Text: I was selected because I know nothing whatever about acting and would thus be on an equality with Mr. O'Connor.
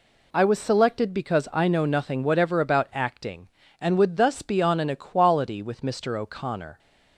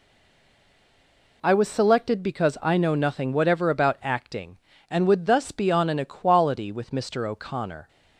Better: first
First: none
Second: stays silent before the first word; noticeable; until 1.4 s; 1.4 s long

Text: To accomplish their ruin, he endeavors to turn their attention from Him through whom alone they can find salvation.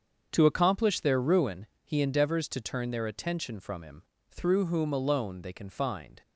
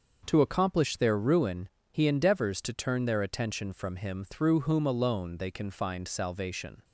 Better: second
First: starts louder than the rest; strong; until 1.3 s; 7 dB // pauses between "Him" and "through"; slight; at 4.0 s; 0.26 s long // stops before "salvation"; at 6.2 s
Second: starts louder than the rest; until 1.2 s; 6.5 dB

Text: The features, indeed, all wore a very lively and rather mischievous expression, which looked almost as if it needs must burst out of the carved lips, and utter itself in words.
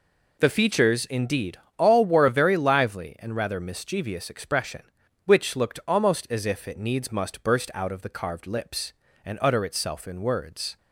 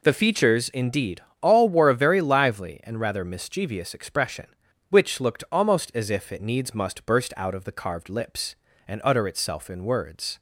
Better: neither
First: none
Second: none

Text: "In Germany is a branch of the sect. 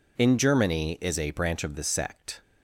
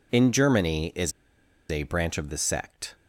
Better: first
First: none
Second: pauses between "is" and "a"; noticeable; at 1.1 s; 0.59 s long

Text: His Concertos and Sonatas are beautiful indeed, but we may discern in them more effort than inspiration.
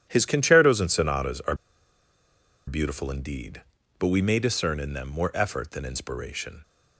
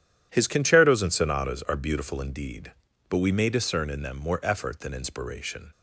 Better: second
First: pauses between "are" and "beautiful"; at 1.5 s; 1.1 s long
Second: none

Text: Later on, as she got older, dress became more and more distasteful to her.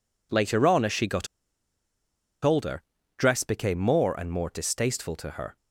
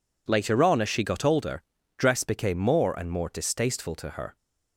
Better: second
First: pauses between "got" and "older"; at 1.2 s; 1.1 s long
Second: none

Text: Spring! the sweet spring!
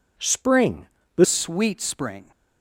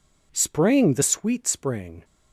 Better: second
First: changes voice at "sweet"; from 1.2 s on; 1.1 s long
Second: none

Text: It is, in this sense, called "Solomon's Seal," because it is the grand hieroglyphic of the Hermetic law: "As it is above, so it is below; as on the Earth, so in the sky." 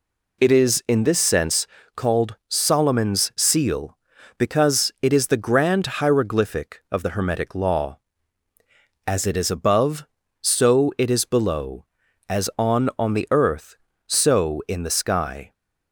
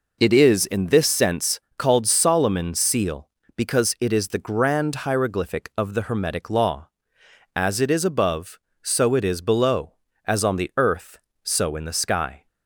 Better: second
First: says "on" twice; at 12.9 s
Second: none

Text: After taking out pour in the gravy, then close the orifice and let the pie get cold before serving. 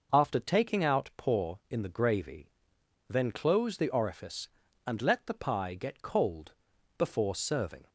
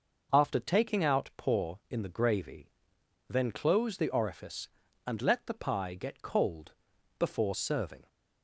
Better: neither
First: pauses between "cold" and "before"; at 6.5 s; 0.43 s long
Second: pauses between "cold" and "before"; at 6.7 s; 0.44 s long

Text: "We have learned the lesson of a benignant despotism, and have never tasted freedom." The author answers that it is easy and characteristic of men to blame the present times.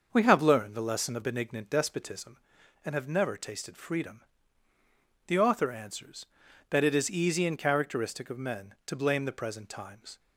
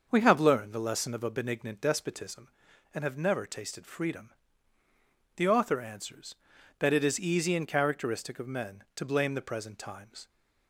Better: second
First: starts louder than the rest; until 1.1 s; 6.5 dB // skips "a"; at 1.2 s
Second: starts louder than the rest; until 1.1 s; 6.5 dB

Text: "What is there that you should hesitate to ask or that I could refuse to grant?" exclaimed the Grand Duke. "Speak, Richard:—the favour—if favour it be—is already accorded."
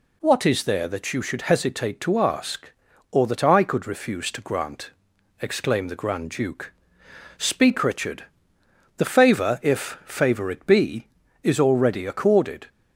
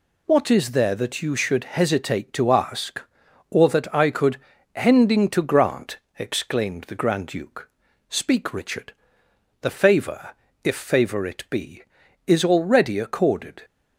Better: first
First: none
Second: says "hending" for "refuse"; at 4.7 s

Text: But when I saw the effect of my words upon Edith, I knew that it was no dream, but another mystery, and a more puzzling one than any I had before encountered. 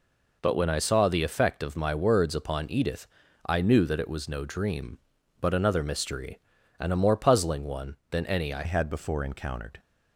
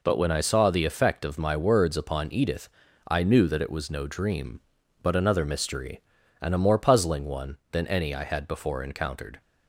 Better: second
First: changes voice at "had"; from 8.6 s on; 1.1 s long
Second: none

